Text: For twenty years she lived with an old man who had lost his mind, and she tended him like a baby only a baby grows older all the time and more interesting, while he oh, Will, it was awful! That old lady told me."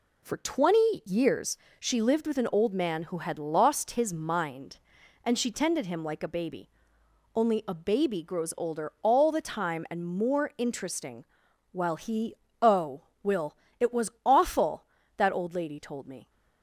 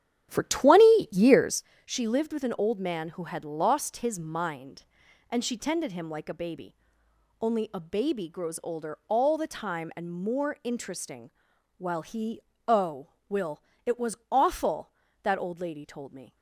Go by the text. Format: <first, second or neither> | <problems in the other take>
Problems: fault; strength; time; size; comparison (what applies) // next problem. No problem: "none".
first | starts louder than the rest; strong; until 1.7 s; 10.5 dB // pauses between "years" and "she"; slight; at 1.6 s; 0.20 s long; slight in the first // pauses between "baby" and "only"; noticeable; at 6.7 s; 0.66 s long; noticeable in the first // pauses between "he" and "oh"; slight; at 12.4 s; 0.26 s long; slight in the first